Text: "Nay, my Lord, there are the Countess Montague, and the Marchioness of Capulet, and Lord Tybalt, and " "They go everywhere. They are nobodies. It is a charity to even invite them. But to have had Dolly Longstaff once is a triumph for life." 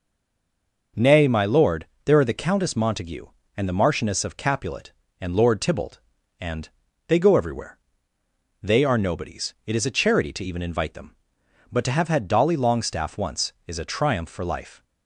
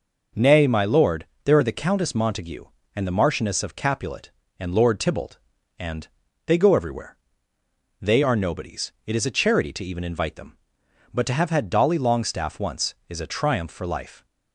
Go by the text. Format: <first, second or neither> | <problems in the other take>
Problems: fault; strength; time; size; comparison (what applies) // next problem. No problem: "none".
second | stays silent before the first word; slight; until 0.9 s; 0.9 s long